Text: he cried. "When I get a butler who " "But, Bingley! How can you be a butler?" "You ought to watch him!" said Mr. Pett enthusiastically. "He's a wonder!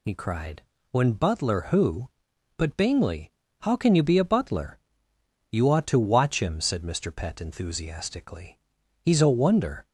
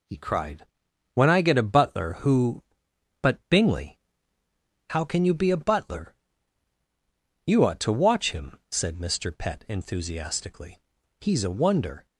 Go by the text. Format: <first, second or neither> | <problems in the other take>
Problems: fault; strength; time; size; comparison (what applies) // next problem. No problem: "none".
second | skips "I get a"; at 1.1 s